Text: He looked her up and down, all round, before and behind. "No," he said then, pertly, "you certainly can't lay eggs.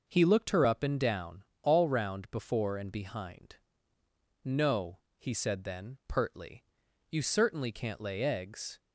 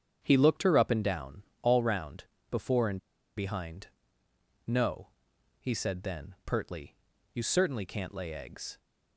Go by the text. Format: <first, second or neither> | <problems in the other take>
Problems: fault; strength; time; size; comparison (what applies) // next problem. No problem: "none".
first | starts louder than the rest; strong; until 1.2 s; 8 dB // pauses between "and" and "behind"; at 2.9 s; 0.38 s long